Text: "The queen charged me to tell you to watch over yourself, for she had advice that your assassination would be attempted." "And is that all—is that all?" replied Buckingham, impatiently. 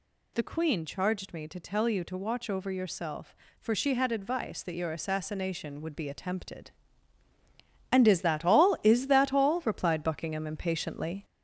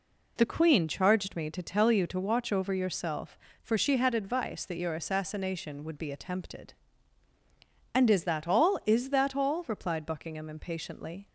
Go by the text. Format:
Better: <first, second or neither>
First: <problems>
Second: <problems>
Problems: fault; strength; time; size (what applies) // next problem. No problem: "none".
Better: second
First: gets louder; noticeable; throughout; 4 dB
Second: none